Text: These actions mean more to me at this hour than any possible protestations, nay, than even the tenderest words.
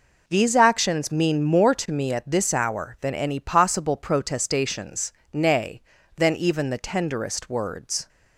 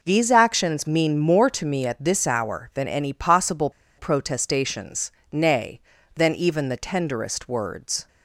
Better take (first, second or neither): first